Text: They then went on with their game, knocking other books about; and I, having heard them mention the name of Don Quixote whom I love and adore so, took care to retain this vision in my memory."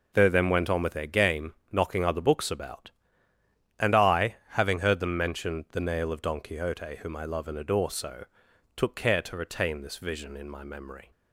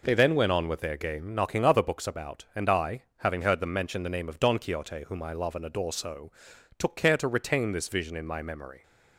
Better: second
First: says "nail" for "name"; at 5.8 s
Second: none

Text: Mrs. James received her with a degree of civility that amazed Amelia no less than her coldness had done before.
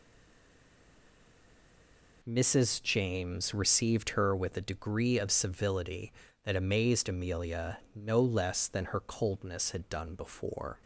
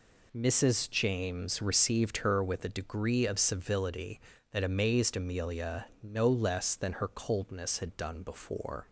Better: second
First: stays silent before the first word; until 2.2 s; 2.2 s long // pauses between "Amelia" and "no"; slight; at 7.7 s; 0.16 s long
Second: pauses between "Amelia" and "no"; slight; at 5.8 s; 0.16 s long

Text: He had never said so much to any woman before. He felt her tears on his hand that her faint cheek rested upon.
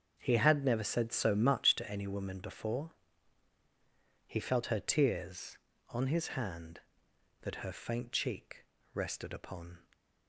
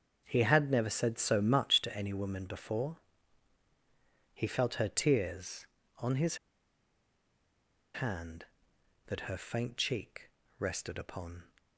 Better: first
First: starts louder than the rest; until 1.1 s; 7 dB // pauses between "cheek" and "rested"; slight; at 8.6 s; 0.30 s long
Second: starts louder than the rest; until 1.2 s; 7 dB // pauses between "his" and "hand"; strong; at 6.3 s; 1.5 s long // pauses between "cheek" and "rested"; slight; at 10.2 s; 0.30 s long

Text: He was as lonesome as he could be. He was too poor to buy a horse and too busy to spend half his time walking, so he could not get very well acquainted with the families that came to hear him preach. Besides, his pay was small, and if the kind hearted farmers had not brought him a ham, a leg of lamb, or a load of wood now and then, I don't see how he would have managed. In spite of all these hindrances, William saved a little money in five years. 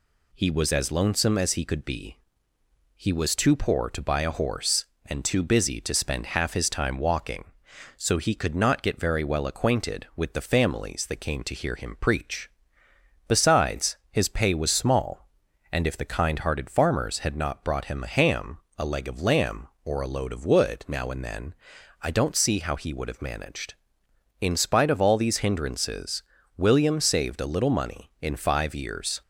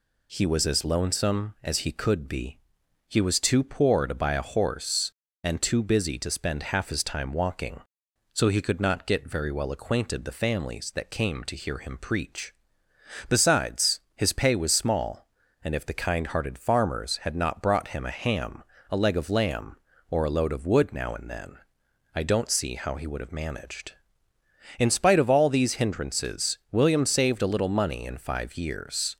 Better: first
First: none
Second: skips "with"; at 10.2 s

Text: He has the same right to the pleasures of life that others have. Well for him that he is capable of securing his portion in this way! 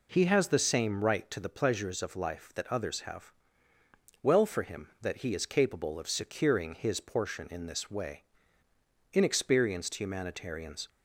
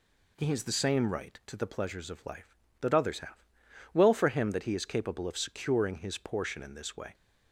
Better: second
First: goes on to say "Inexperienced humanitarians"; strong; from 9.1 s on; 1.7 s long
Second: none

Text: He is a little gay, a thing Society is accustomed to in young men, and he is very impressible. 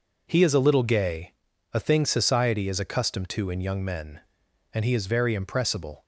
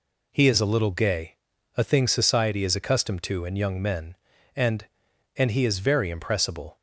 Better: first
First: none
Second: says "and" twice; at 5.3 s

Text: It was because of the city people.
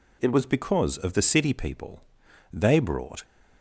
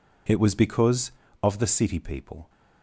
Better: second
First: goes on to say "They brought"; noticeable; from 2.5 s on; 0.72 s long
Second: none

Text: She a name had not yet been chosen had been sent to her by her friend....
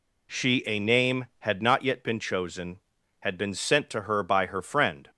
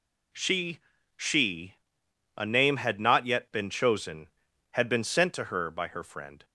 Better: first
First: none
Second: says "She" twice; at 1.1 s

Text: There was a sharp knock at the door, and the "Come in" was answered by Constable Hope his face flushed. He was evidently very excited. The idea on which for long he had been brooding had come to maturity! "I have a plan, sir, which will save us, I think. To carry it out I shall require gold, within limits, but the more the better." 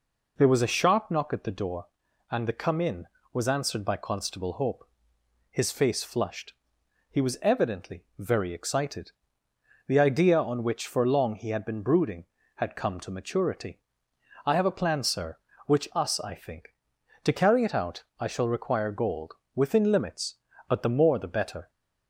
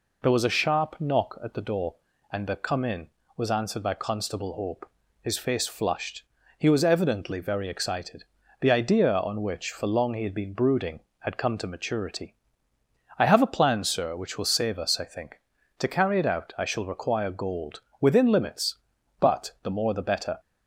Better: second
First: pauses between "Hope" and "his"; noticeable; at 4.8 s; 0.64 s long // skips "will save"; at 15.9 s // pauses between "out" and "I"; slight; at 18.0 s; 0.16 s long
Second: pauses between "Hope" and "his"; slight; at 4.8 s; 0.32 s long

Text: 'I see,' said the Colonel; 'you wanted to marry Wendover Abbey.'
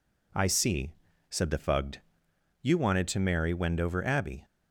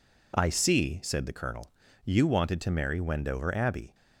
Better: second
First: says "Fugged" for "Colonel"; at 1.5 s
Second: none

